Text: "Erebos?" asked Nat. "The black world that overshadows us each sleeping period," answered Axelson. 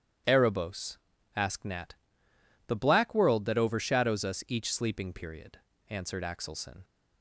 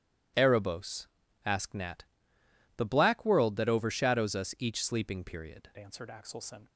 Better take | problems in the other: first | starts louder than the rest; strong; until 1.7 s; 11.5 dB; strong in the first // changes voice at "answered"; from 5.7 s on; 0.9 s long

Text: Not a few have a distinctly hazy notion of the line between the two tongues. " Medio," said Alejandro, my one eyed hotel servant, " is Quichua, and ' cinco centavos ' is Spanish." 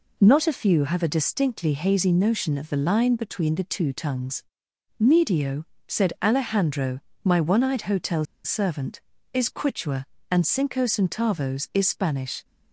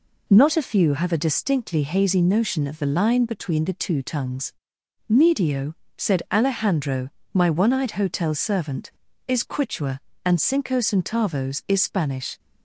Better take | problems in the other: second | pauses between "hotel" and "servant"; slight; at 8.2 s; 0.19 s long

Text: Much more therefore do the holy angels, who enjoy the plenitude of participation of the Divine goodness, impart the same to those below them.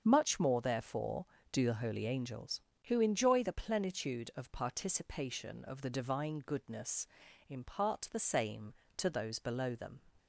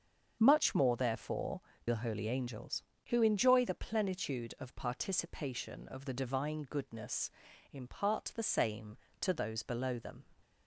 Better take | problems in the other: first | starts louder than the rest; until 1.4 s; 7 dB; also in the first // skips "do"; at 1.7 s

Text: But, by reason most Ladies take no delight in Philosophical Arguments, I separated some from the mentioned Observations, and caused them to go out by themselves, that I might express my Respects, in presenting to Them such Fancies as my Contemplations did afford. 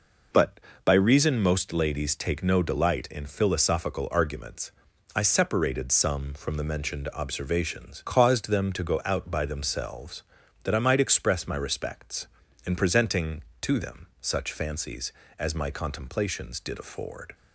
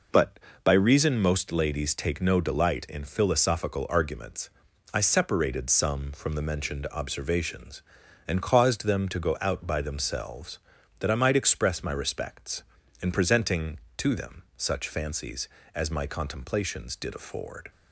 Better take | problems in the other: second | skips "and"; at 8.0 s

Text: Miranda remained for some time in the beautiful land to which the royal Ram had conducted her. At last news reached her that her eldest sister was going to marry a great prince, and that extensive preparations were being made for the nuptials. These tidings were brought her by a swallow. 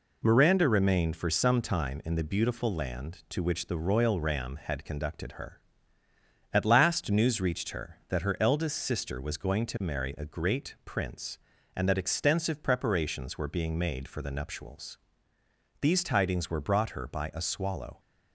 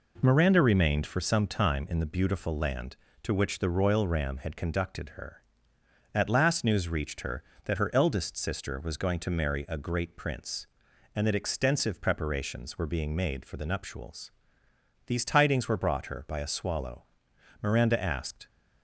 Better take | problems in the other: first | goes on to say "Miranda asked"; noticeable; from 17.6 s on; 0.86 s long

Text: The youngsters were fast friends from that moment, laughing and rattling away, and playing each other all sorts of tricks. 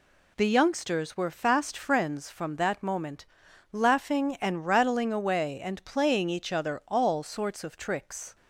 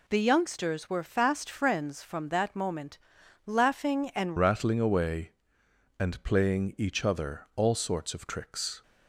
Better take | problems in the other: first | changes voice at "rattling"; from 4.3 s on; 4.5 s long

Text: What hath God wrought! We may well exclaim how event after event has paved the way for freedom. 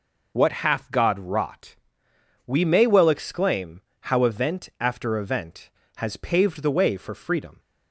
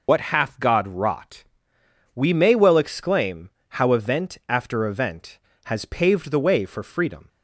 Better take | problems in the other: first | loses the start of "What"; at 0.0 s; 70 ms // pauses between "exclaim" and "how"; slight; at 3.4 s; 0.20 s long; slight in the first

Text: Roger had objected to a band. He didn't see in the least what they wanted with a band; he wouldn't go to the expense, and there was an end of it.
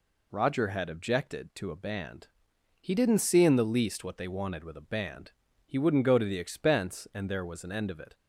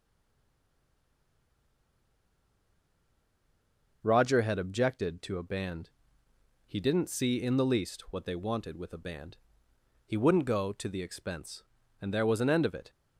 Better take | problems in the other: first | stays silent before the first word; strong; until 4.0 s; 4.0 s long

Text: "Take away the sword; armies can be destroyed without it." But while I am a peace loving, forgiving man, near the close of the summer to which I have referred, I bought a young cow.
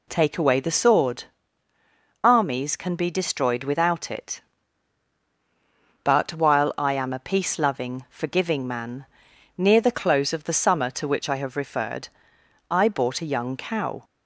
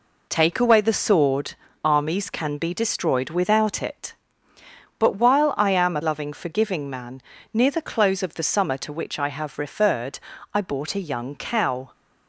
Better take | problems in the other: first | skips "peace"; at 6.0 s

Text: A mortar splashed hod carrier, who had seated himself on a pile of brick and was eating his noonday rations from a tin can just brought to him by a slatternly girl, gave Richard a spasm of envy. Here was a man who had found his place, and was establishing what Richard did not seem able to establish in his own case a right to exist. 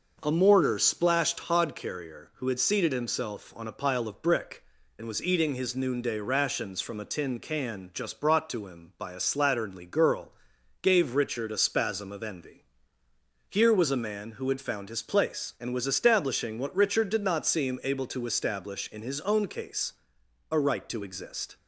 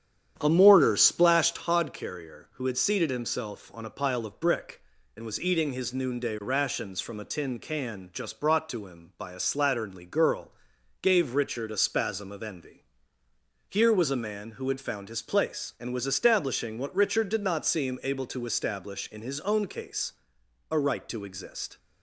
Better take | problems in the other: first | starts louder than the rest; strong; until 1.7 s; 9 dB // pauses between "case" and "a"; noticeable; at 20.1 s; 0.58 s long; noticeable in the first

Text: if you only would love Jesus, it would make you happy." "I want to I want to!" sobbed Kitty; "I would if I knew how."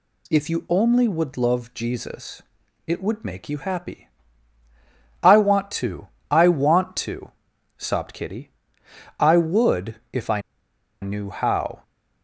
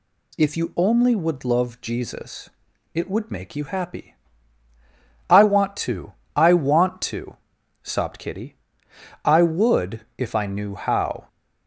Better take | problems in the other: second | pauses between "to" and "I"; slight; at 6.0 s; 0.20 s long; slight in the second // pauses between "I" and "knew"; noticeable; at 10.4 s; 0.61 s long

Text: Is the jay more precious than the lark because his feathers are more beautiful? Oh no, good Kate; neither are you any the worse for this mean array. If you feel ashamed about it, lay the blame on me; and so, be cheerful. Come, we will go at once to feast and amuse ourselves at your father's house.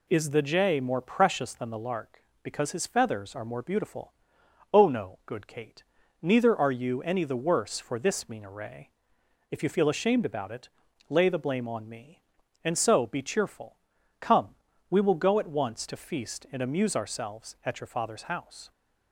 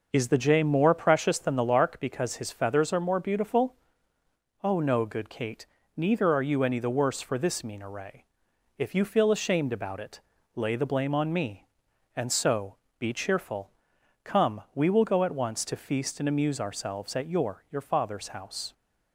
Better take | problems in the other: first | says "your" twice; at 17.6 s

